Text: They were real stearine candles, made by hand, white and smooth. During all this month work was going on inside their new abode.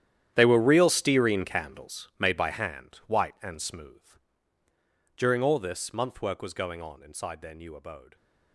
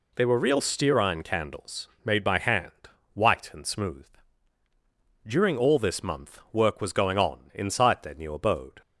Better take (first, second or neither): second